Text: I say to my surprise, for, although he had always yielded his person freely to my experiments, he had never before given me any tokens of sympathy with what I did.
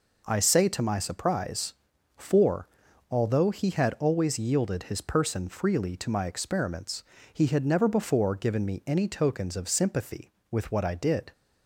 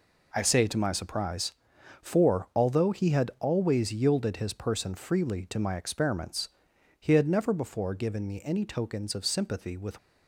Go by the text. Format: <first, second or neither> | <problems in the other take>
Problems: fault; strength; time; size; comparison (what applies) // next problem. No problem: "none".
first | stops before "what I did"; at 9.9 s